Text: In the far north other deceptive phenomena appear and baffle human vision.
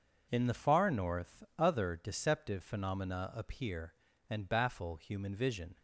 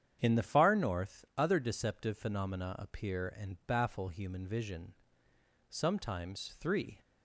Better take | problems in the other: first | starts louder than the rest; strong; until 1.2 s; 8.5 dB // goes on to say "Sometimes three"; noticeable; from 5.6 s on; 1.3 s long

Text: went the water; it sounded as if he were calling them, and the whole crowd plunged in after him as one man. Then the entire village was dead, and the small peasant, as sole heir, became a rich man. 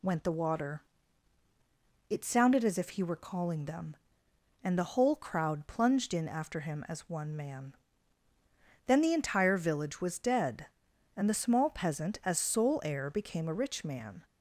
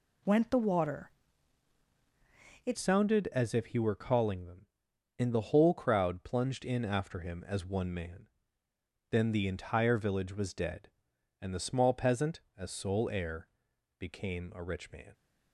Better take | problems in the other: first | changes voice at "sounded"; from 2.7 s on; 12.4 s long

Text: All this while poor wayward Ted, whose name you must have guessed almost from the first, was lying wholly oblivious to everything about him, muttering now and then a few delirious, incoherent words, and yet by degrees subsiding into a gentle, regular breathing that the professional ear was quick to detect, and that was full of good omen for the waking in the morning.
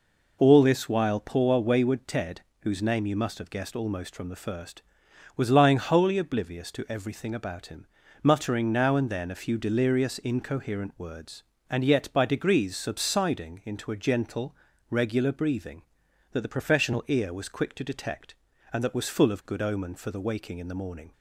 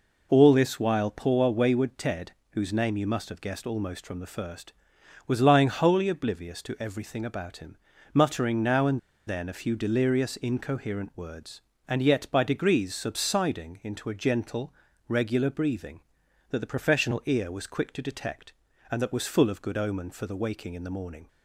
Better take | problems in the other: first | pauses between "and" and "then"; slight; at 8.9 s; 0.27 s long

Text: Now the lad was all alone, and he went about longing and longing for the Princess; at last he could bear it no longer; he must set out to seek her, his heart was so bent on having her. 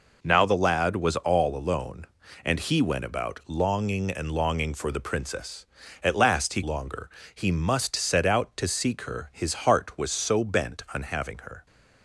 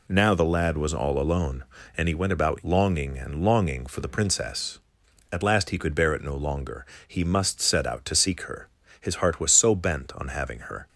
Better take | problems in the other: second | skips "could bear it no"; at 6.6 s

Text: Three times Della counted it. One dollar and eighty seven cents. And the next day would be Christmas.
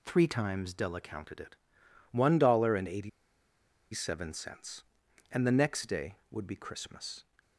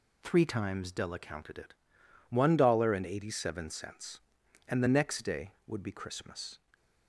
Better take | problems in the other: second | pauses between "eighty" and "seven"; noticeable; at 3.0 s; 0.84 s long

